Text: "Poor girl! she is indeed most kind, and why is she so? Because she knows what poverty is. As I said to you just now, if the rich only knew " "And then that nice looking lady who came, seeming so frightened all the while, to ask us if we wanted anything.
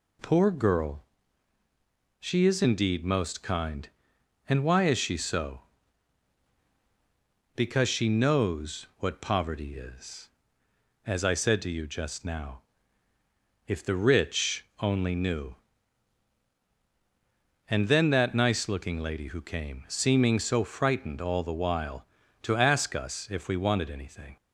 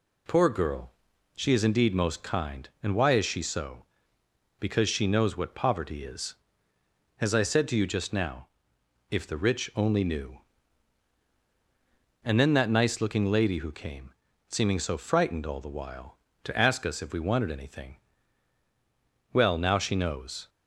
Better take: first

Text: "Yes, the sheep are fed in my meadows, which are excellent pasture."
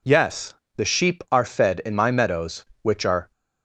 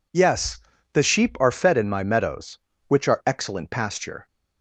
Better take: second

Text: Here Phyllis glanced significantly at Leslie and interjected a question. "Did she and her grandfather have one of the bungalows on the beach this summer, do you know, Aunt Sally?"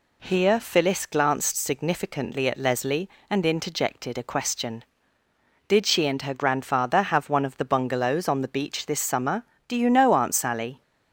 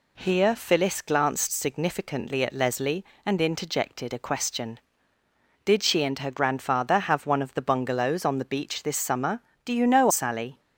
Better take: first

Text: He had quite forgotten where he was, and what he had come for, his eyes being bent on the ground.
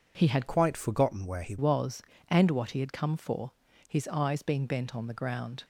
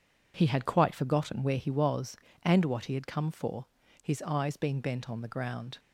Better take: second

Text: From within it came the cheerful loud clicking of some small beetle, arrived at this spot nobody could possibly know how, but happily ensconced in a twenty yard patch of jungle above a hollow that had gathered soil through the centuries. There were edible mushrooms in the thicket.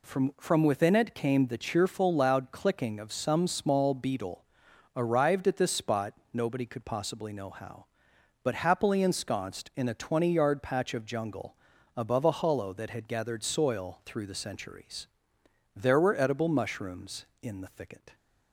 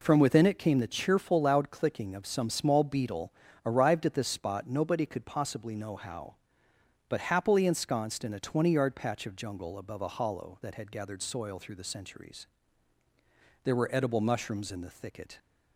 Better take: second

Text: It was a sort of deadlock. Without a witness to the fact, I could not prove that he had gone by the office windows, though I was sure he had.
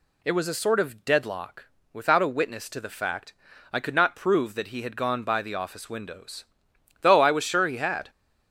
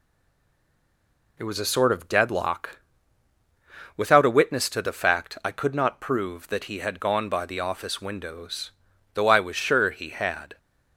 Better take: first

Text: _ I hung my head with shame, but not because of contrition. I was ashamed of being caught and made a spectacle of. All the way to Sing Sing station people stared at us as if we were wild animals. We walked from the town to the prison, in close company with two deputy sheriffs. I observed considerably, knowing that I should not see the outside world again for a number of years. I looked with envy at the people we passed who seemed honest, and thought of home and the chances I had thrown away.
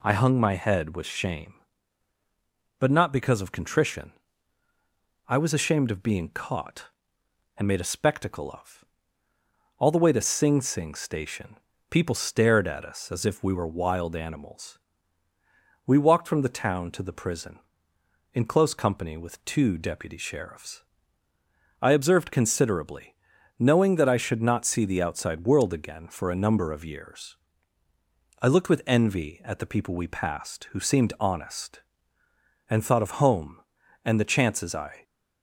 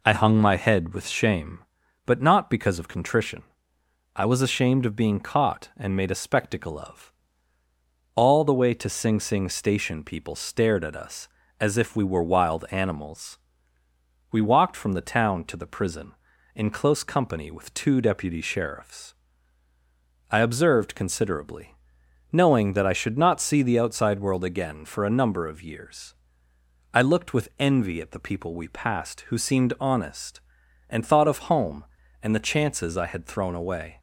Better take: second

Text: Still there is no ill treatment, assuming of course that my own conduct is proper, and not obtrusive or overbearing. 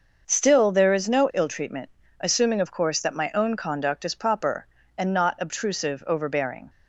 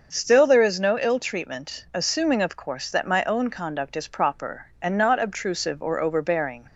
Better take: second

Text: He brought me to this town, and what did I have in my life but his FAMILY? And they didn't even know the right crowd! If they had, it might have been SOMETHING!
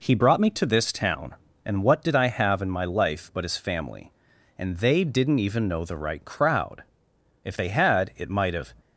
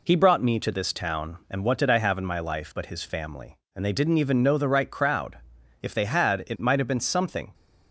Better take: second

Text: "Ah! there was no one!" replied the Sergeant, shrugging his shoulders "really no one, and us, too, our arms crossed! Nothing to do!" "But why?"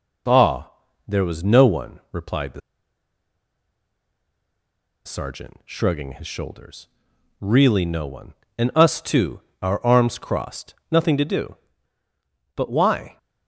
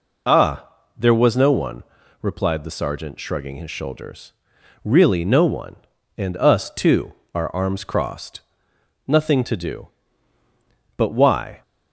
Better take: second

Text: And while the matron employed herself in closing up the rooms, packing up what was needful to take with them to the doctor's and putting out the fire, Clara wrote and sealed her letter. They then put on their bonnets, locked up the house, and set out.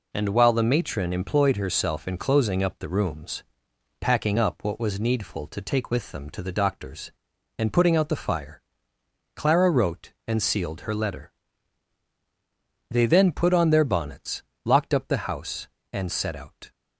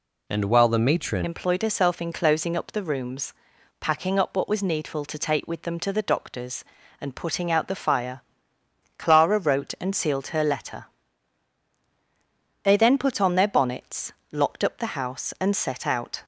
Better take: first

